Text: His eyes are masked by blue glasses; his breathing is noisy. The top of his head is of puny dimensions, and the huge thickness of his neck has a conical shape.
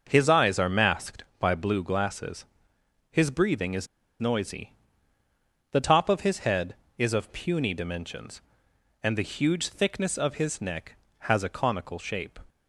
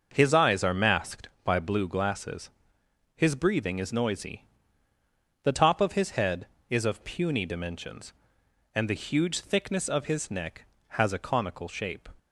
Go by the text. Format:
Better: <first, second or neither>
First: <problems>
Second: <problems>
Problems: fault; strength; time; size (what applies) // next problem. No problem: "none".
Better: second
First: starts louder than the rest; noticeable; until 1.0 s; 6 dB // pauses between "is" and "noisy"; slight; at 3.8 s; 0.35 s long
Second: starts louder than the rest; noticeable; until 1.1 s; 6 dB